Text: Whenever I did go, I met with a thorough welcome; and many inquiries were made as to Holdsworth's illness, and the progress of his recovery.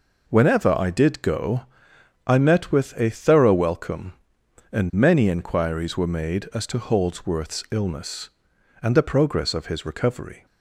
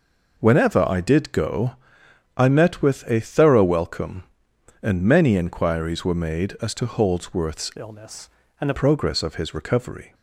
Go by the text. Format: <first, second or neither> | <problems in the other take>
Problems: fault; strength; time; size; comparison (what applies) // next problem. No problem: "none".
first | changes voice from "illness" to "the"; from 7.7 to 8.7 s; 1.0 s long